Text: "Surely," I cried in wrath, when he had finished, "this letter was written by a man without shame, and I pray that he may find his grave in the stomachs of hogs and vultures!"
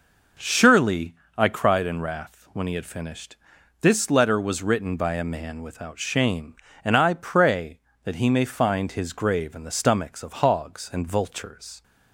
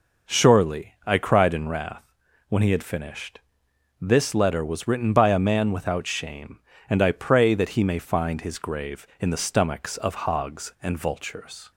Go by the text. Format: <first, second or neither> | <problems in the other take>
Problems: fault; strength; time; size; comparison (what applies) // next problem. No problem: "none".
neither | none